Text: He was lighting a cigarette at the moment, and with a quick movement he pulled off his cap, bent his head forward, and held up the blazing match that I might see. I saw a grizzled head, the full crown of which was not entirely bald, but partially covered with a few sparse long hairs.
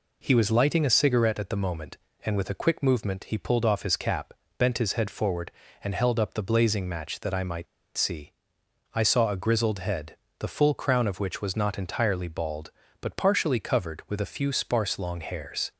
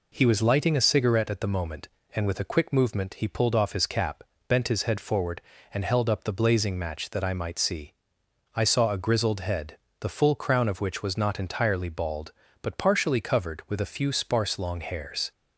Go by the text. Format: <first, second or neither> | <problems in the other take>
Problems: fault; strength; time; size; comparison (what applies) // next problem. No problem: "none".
second | pauses between "might" and "see"; slight; at 7.6 s; 0.30 s long